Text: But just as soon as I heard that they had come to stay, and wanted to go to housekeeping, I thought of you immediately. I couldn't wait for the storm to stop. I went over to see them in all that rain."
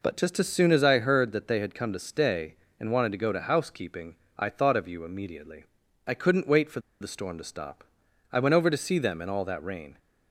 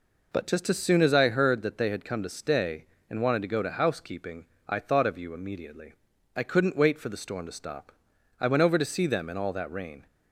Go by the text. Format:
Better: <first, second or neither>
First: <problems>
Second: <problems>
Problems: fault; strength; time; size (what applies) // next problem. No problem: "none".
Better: second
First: pauses between "for" and "the"; slight; at 6.8 s; 0.20 s long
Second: none